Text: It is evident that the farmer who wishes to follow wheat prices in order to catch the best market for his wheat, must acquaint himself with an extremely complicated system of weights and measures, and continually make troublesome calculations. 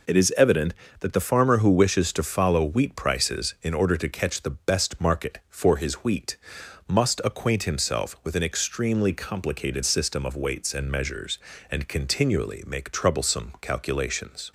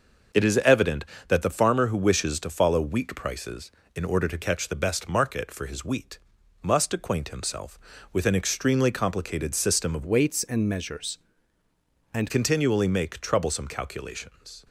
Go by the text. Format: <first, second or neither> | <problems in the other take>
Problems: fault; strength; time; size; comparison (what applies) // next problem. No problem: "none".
first | changes voice from "weights" to "and"; from 10.0 to 12.3 s; 2.3 s long